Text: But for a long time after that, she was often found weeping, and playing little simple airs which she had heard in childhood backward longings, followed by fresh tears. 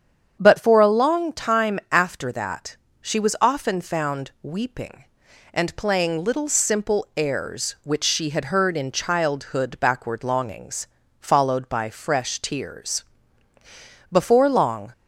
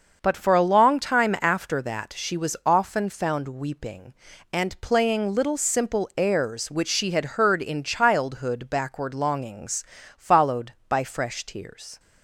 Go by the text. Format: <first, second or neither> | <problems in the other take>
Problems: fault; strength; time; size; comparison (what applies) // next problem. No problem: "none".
second | starts louder than the rest; strong; until 1.4 s; 8 dB; also in the second // goes on to say "Before long"; noticeable; from 14.1 s on; 0.80 s long